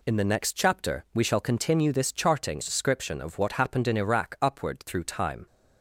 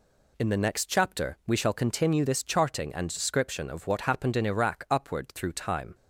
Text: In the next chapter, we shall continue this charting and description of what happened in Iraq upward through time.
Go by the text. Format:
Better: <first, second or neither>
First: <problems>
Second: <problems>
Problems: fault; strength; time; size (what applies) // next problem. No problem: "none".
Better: second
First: skips "and"; at 2.6 s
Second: none